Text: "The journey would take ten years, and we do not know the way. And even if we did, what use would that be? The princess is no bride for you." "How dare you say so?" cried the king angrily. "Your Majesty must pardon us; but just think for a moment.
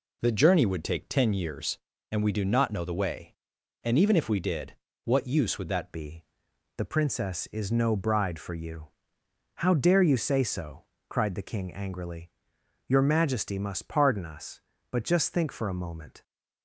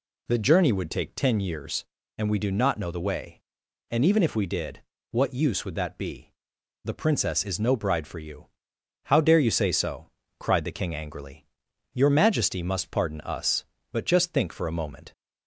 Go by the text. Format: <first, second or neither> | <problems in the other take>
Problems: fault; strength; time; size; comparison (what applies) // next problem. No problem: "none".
second | changes voice at "be"; from 5.9 s on; 10.3 s long